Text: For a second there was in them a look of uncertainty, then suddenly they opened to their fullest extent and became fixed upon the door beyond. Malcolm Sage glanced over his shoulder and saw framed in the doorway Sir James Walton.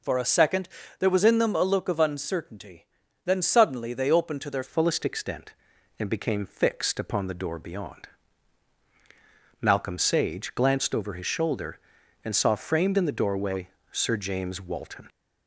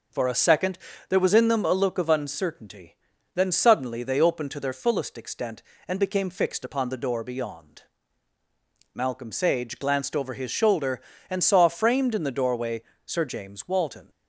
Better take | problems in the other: second | pauses between "second" and "there"; slight; at 0.6 s; 0.30 s long; slight in the second // changes voice at "fullest"; from 4.6 s on; 10.4 s long // pauses between "doorway" and "Sir"; slight; at 13.6 s; 0.22 s long; slight in the second

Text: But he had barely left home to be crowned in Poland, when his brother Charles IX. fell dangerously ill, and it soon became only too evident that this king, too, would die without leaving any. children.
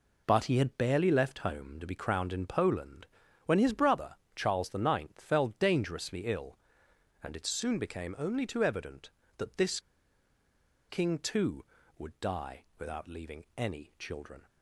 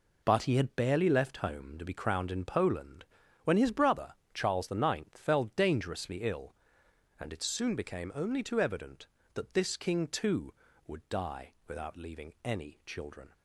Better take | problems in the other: second | pauses between "brother" and "Charles"; slight; at 4.1 s; 0.20 s long; slight in the second // pauses between "this" and "king"; at 9.7 s; 1.0 s long

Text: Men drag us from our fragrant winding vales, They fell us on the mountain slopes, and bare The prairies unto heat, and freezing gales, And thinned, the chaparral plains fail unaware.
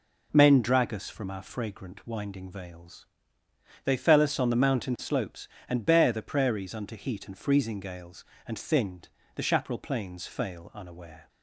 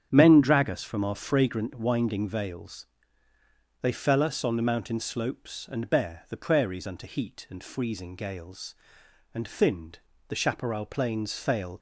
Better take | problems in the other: first | starts louder than the rest; strong; until 1.1 s; 8.5 dB // stops before "unaware"; at 11.7 s

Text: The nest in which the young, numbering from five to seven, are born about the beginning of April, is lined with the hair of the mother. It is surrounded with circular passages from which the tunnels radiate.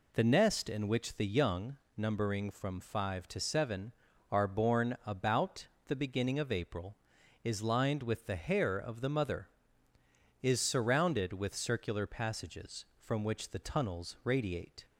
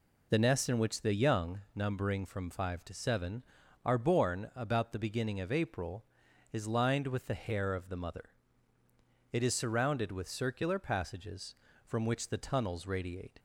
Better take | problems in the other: second | pauses between "about" and "the"; slight; at 5.6 s; 0.20 s long // skips "It"; at 9.9 s

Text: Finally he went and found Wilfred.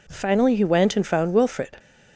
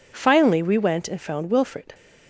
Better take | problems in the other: first | says "we" for "he"; at 0.6 s

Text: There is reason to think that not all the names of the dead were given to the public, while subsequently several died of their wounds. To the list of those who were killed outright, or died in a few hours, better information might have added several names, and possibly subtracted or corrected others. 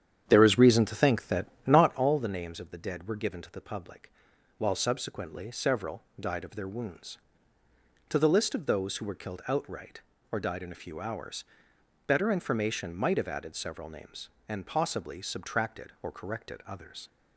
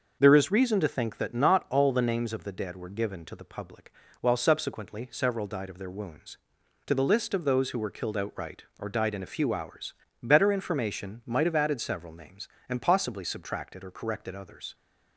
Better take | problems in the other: second | starts louder than the rest; strong; until 2.1 s; 9 dB // pauses between "that" and "not"; slight; at 1.4 s; 0.22 s long // pauses between "several" and "died"; slight; at 6.0 s; 0.18 s long

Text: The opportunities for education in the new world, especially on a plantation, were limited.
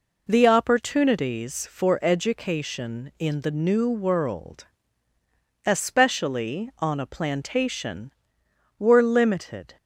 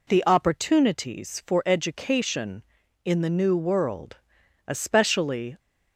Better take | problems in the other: first | stops before "on a plantation were limited"; at 5.5 s

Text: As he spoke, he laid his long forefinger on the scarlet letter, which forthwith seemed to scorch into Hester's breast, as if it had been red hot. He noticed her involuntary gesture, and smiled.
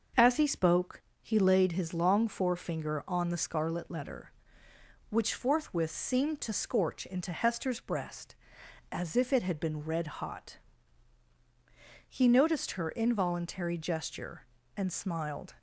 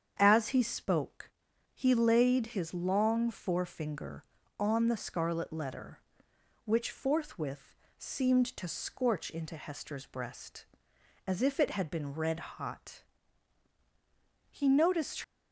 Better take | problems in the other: first | starts louder than the rest; strong; until 1.2 s; 8 dB; also in the first // pauses between "forthwith" and "seemed"; slight; at 7.7 s; 0.24 s long // stops before "her involuntary gesture and smiled"; at 15.2 s

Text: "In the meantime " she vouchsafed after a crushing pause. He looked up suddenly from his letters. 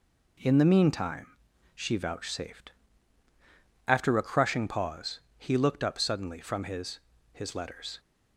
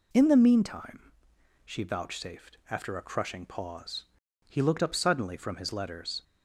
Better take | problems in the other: second | pauses between "vouchsafed" and "after"; at 2.7 s; 1.1 s long // says "his" twice; at 7.3 s

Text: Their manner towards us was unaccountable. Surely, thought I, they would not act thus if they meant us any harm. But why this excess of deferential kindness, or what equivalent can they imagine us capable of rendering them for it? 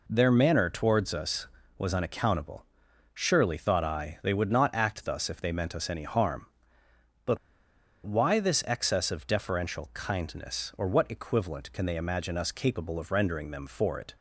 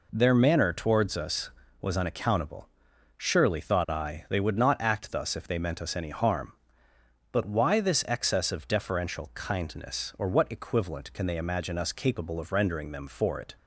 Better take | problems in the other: second | pauses between "But" and "why"; noticeable; at 7.3 s; 0.67 s long

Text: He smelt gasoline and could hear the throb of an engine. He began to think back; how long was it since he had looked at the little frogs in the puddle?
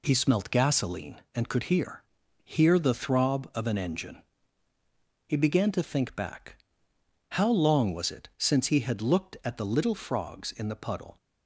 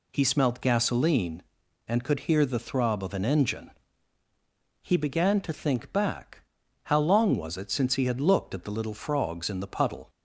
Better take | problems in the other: second | says "hear" twice; at 2.4 s

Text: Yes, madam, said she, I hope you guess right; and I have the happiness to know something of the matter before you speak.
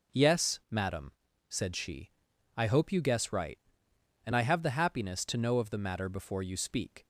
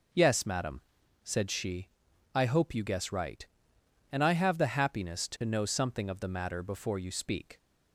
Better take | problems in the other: second | skips "something"; at 5.5 s

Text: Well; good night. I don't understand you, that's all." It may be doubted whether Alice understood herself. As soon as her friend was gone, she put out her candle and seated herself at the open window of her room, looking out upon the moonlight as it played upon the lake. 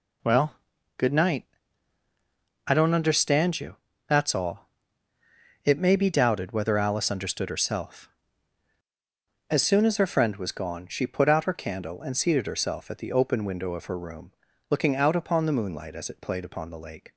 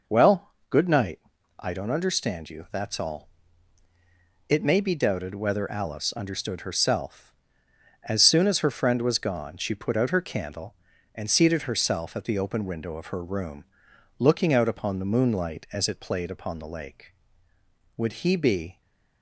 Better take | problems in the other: first | goes on to say "Would he be"; noticeable; from 17.9 s on; 0.84 s long

